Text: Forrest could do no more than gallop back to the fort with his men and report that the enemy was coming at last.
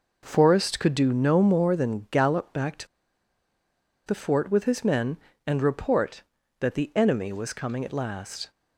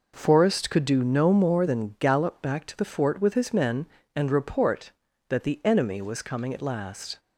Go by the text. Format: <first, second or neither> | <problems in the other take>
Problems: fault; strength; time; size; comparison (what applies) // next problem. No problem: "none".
second | pauses between "to" and "the"; at 2.8 s; 1.1 s long